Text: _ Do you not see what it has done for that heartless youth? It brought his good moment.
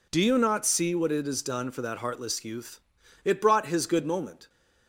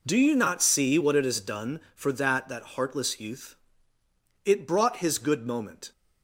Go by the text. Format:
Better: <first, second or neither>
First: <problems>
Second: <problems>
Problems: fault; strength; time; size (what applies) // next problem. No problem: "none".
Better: first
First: none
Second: says "that" twice; at 2.4 s